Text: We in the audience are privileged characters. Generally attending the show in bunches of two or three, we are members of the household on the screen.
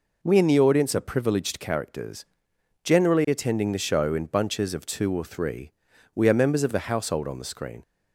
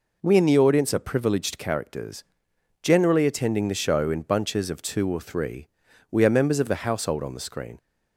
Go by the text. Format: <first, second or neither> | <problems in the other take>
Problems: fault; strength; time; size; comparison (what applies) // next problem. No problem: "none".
neither | none